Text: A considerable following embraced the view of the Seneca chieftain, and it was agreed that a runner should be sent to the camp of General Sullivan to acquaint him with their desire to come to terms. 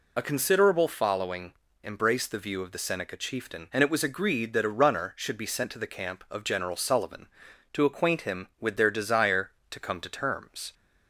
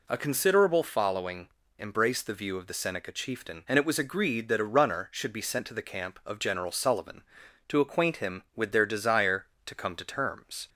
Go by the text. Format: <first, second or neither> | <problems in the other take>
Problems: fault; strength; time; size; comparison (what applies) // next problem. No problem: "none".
second | loses the start of "A"; at 0.1 s; 50 ms // pauses between "following" and "embraced"; slight; at 1.5 s; 0.30 s long; slight in the second